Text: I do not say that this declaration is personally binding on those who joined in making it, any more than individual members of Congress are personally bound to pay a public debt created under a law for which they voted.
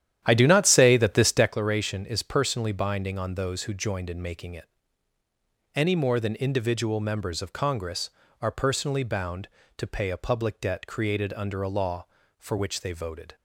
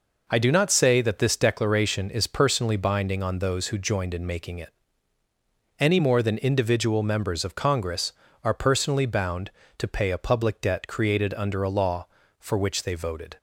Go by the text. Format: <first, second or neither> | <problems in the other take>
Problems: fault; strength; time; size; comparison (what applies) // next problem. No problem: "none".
second | starts louder than the rest; strong; until 1.6 s; 11 dB